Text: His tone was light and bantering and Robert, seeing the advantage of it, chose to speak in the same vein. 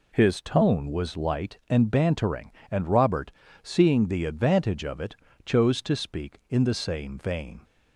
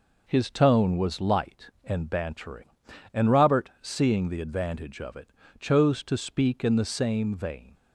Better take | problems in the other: neither | none

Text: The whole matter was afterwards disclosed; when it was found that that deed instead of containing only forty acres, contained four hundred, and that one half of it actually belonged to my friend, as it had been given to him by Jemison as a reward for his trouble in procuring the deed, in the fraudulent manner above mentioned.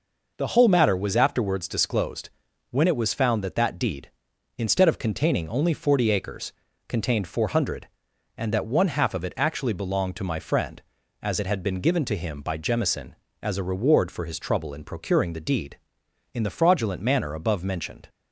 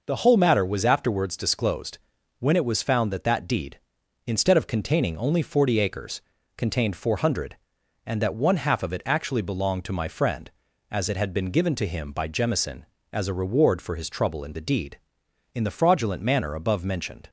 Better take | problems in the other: first | skips "procuring"; at 14.5 s

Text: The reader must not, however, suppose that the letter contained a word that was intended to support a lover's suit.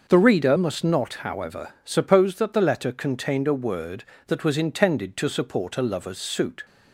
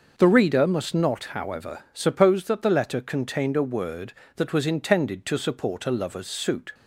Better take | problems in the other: neither | none

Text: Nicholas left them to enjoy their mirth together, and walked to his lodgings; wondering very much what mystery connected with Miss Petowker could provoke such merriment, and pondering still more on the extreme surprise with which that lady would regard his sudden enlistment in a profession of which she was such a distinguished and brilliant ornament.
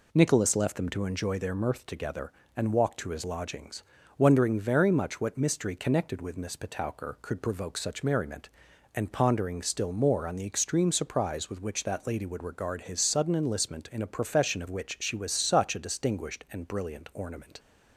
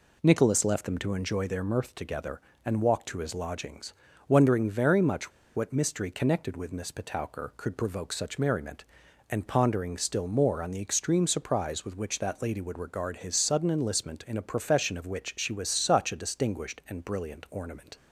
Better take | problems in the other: first | pauses between "much" and "what"; slight; at 5.3 s; 0.25 s long

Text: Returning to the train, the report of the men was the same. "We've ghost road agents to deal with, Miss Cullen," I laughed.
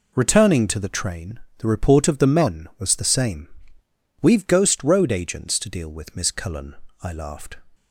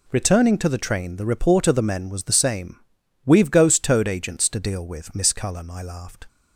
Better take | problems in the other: first | says "toad" for "road"; at 3.8 s

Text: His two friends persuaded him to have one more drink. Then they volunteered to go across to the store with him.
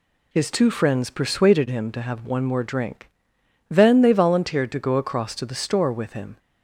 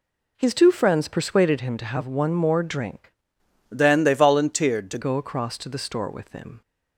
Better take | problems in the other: first | changes voice from "Then" to "to"; from 3.7 to 4.9 s; 1.2 s long

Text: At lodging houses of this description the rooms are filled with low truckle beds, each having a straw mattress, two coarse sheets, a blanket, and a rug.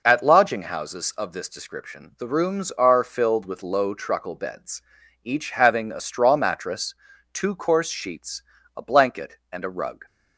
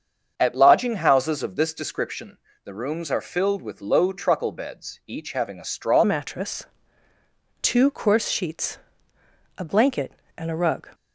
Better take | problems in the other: first | starts louder than the rest; until 1.3 s; 7 dB // pauses between "description" and "the"; slight; at 2.3 s; 0.28 s long // changes voice at "mattress"; from 6.0 s on; 4.8 s long

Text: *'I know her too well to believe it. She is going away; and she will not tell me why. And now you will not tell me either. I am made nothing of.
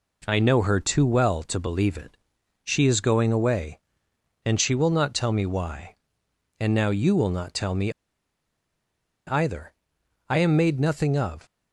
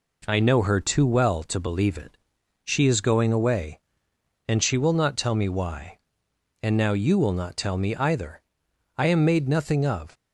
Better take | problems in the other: second | pauses between "me" and "either"; strong; at 7.9 s; 1.3 s long

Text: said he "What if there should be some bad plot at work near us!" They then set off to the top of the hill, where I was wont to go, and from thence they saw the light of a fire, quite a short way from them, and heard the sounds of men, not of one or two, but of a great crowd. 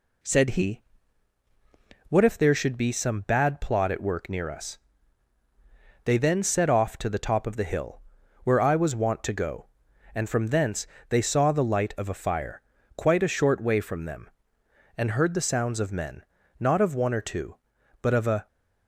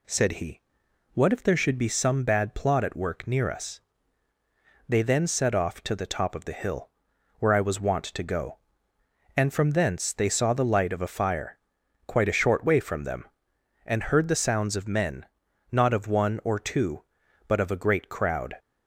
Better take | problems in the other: second | pauses between "he" and "What"; strong; at 0.8 s; 1.2 s long; noticeable in the second // pauses between "thence" and "they"; slight; at 10.8 s; 0.22 s long // stops before "great crowd"; at 18.4 s

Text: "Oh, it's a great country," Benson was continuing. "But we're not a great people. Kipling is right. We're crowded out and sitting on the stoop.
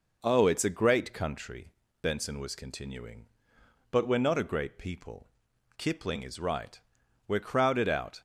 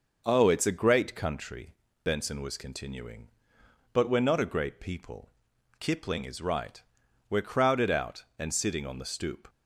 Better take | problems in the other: second | stops before "and sitting on the stoop"; at 8.1 s

